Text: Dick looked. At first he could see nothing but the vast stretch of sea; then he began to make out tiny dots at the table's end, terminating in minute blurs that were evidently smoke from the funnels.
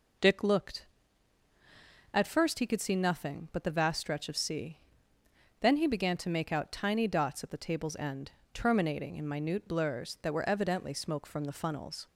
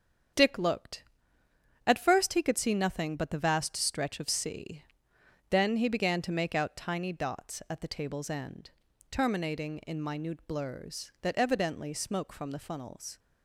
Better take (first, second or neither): first